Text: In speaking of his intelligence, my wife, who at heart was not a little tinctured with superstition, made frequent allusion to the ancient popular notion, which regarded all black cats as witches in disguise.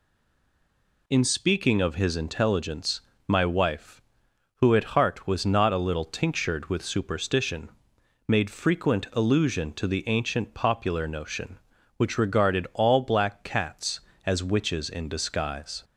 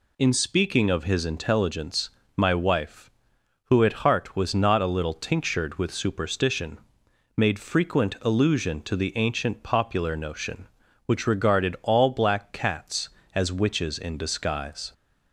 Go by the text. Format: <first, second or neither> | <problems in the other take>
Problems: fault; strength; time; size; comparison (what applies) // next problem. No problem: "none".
second | stays silent before the first word; until 1.0 s; 1.0 s long